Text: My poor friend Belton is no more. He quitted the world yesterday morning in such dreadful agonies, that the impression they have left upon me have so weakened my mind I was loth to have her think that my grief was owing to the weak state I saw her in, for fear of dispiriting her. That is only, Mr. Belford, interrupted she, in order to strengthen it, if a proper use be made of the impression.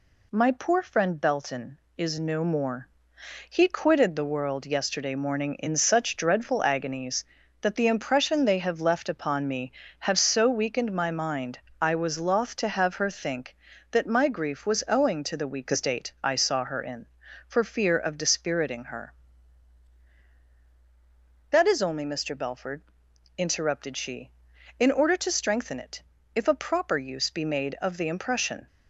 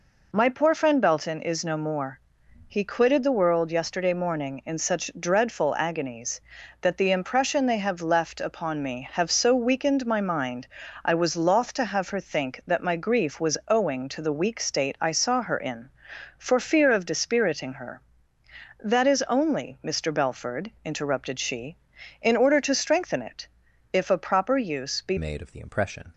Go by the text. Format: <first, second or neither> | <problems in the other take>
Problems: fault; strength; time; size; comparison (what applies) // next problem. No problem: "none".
first | pauses between "mind" and "I"; at 10.6 s; 0.38 s long; slight in the first // changes voice at "made"; from 25.1 s on; 1.0 s long